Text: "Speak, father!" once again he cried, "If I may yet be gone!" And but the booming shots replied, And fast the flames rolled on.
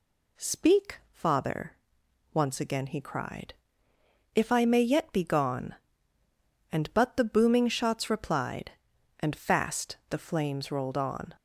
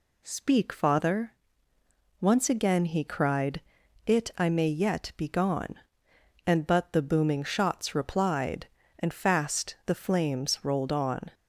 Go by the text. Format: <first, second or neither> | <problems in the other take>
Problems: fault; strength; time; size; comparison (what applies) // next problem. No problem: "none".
first | says "It" for "If"; at 4.0 s